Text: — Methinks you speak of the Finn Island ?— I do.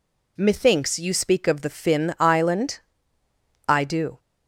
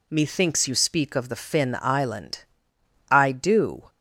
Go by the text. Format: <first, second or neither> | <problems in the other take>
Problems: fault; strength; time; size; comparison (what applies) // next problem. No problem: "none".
neither | none